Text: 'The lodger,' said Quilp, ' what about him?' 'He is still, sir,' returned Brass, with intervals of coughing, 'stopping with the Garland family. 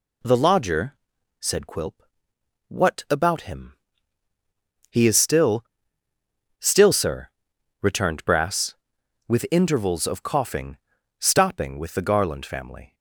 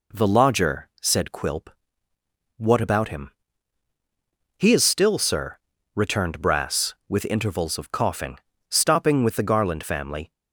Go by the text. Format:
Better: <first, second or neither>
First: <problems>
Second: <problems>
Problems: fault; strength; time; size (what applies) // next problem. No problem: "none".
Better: second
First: says "still" twice; at 6.5 s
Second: none